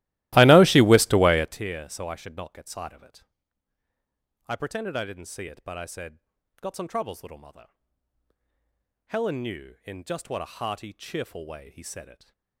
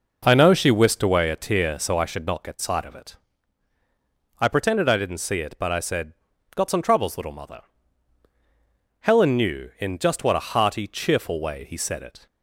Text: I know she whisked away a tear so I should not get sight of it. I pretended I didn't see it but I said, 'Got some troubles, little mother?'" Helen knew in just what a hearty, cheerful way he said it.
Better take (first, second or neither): second